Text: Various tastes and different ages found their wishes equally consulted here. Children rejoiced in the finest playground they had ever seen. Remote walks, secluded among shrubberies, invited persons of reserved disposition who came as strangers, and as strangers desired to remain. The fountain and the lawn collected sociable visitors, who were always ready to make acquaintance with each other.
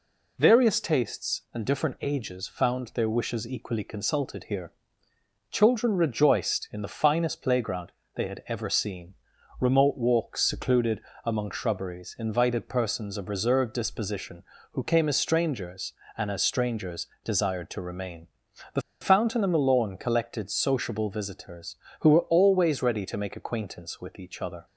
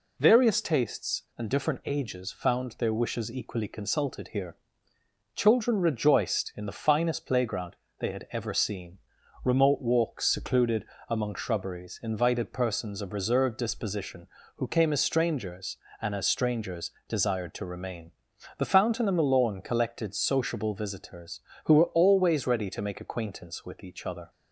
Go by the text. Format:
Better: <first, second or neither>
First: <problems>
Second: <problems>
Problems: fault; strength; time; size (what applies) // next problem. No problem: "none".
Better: second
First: pauses between "playground" and "they"; slight; at 7.9 s; 0.24 s long // pauses between "secluded" and "among"; slight; at 10.9 s; 0.24 s long // pauses between "strangers" and "desired"; slight; at 17.0 s; 0.18 s long // pauses between "The" and "fountain"; slight; at 18.8 s; 0.20 s long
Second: pauses between "playground" and "they"; slight; at 7.7 s; 0.24 s long // pauses between "secluded" and "among"; slight; at 10.8 s; 0.24 s long // pauses between "strangers" and "desired"; slight; at 16.9 s; 0.18 s long